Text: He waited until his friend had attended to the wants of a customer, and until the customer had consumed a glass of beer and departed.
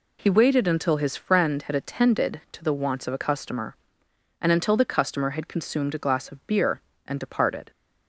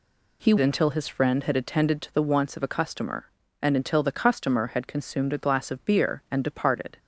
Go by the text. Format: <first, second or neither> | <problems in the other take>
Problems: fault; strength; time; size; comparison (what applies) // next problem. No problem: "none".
first | skips "waited"; at 0.5 s